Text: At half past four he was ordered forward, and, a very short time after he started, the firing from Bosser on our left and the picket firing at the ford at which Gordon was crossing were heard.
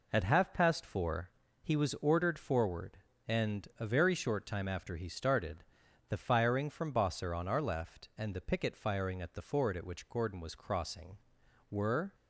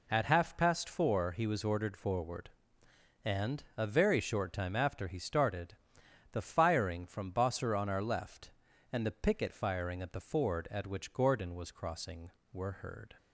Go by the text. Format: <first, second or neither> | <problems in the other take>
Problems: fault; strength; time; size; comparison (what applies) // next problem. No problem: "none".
second | pauses between "four" and "he"; slight; at 1.2 s; 0.32 s long // stops before "heard"; at 12.1 s